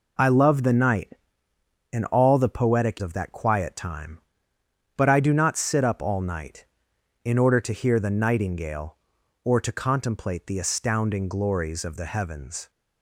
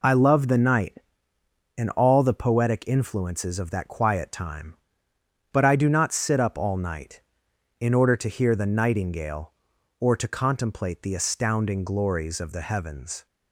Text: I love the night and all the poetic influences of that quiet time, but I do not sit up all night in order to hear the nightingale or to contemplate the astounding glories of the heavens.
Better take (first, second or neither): second